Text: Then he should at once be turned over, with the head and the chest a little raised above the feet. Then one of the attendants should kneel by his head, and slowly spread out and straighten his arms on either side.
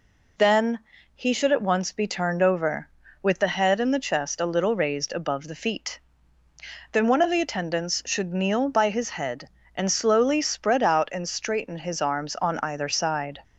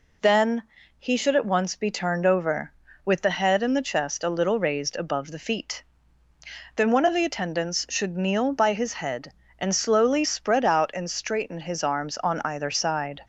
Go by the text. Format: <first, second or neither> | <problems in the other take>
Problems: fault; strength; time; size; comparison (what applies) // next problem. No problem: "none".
neither | pauses between "Then" and "he"; slight; the same in both